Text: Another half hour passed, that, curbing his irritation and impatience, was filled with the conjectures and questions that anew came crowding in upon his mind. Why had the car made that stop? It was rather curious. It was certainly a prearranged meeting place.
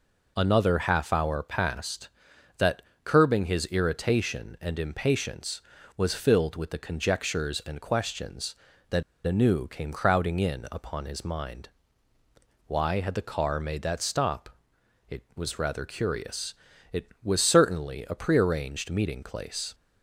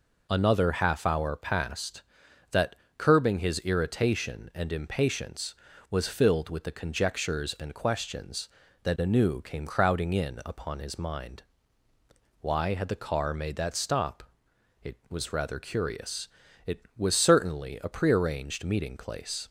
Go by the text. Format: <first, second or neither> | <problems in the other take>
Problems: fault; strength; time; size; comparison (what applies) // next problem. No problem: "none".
second | pauses between "that" and "anew"; slight; at 9.0 s; 0.23 s long